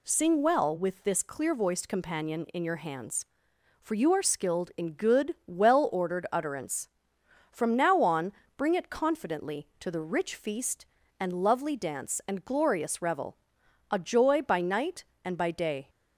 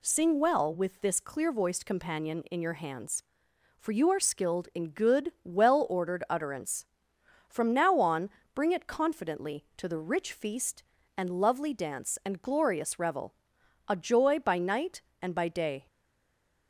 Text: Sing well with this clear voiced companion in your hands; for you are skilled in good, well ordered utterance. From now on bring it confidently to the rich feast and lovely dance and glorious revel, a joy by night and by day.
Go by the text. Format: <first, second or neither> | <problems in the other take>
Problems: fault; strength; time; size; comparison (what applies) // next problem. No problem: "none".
first | pauses between "on" and "bring"; slight; at 8.2 s; 0.24 s long; slight in the first // stays silent after the last word; slight; from 15.8 s on; 0.8 s long